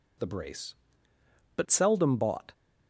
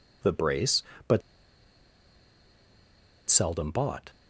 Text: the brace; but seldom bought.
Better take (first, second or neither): first